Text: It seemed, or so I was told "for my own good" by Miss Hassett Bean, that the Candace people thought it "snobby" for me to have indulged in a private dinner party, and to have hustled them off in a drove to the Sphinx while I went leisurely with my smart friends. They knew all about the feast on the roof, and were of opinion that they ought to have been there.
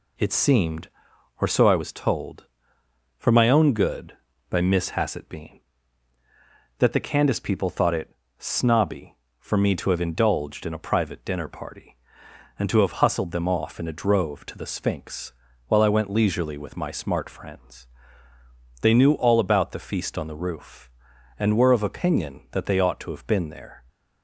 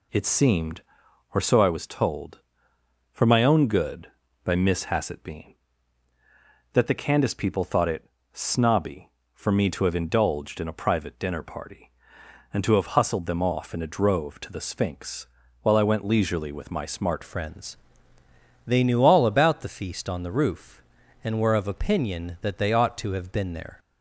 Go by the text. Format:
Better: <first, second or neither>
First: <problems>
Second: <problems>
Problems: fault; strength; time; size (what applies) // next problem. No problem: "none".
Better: first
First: pauses between "it" and "snobby"; slight; at 8.1 s; 0.24 s long // pauses between "Sphinx" and "while"; slight; at 15.3 s; 0.34 s long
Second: pauses between "it" and "snobby"; slight; at 8.0 s; 0.24 s long // pauses between "Sphinx" and "while"; slight; at 15.2 s; 0.34 s long // changes voice at "friends"; from 17.2 s on; 6.5 s long